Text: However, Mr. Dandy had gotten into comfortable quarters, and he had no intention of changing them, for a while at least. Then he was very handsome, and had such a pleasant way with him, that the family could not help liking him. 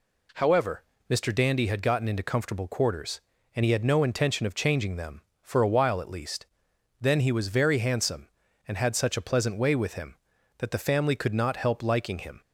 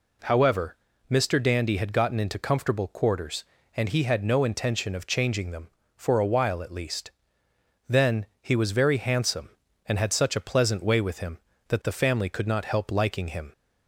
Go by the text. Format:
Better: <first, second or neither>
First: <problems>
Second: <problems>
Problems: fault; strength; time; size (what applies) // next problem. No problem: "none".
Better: neither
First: none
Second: none